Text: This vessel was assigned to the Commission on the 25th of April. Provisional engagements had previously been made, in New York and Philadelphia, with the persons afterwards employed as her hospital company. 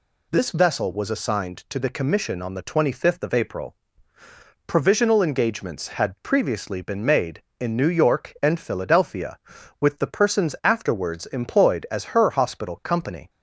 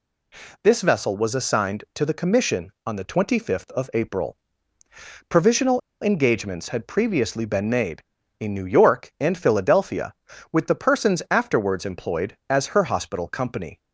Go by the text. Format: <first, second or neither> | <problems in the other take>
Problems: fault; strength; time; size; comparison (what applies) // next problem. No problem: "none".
first | pauses between "Provisional" and "engagements"; slight; at 5.8 s; 0.22 s long